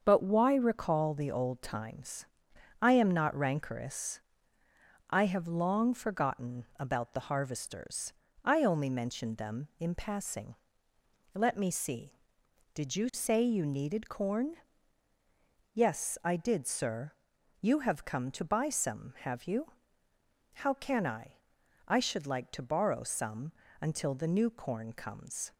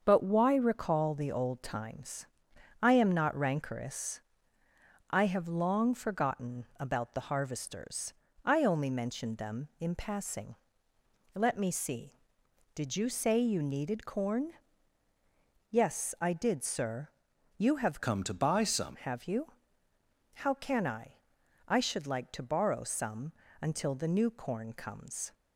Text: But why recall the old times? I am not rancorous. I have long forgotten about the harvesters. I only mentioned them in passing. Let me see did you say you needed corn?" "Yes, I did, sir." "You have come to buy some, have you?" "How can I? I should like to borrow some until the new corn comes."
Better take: first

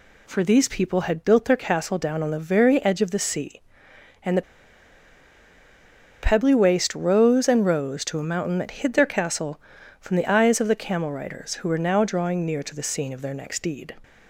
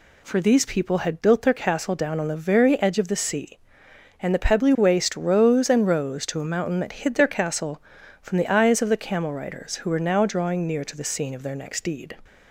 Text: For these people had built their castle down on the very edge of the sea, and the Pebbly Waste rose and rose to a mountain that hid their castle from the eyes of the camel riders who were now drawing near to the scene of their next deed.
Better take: second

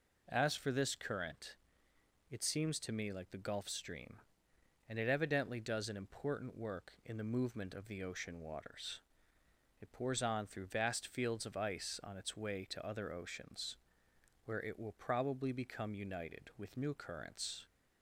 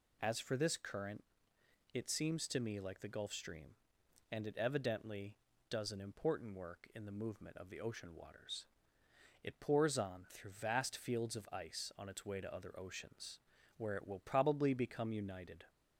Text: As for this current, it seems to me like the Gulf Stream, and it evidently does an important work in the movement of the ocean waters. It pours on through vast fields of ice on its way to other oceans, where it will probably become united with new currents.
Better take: first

